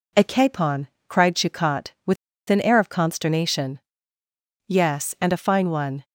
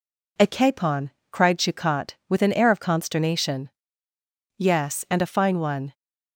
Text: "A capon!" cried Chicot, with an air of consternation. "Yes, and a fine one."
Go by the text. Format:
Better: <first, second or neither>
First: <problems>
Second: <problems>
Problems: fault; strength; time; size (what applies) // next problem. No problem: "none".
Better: second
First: pauses between "with" and "an"; slight; at 2.1 s; 0.34 s long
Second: none